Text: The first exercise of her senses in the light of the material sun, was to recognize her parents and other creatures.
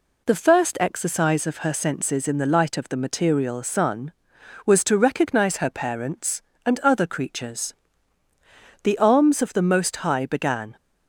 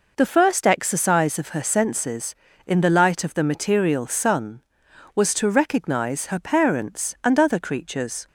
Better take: second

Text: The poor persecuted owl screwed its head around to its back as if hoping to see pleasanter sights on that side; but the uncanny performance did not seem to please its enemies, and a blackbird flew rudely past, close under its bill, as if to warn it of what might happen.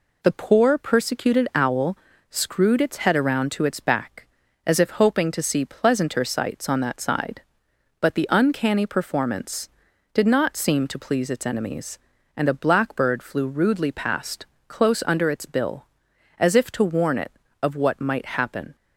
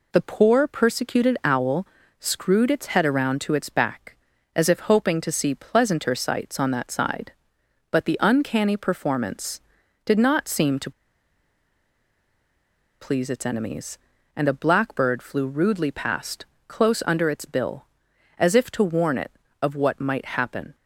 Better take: first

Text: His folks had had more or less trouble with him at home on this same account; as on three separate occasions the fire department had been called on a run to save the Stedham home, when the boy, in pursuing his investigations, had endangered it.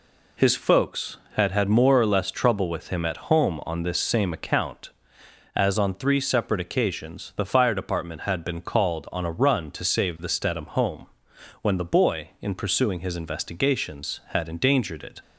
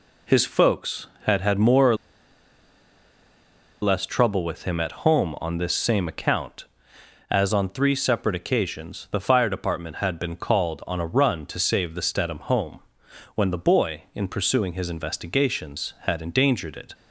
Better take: first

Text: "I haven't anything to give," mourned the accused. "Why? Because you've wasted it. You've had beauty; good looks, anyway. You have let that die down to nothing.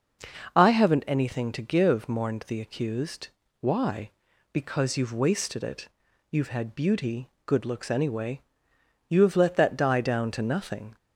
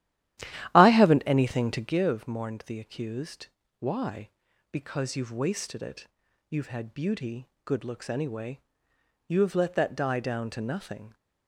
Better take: first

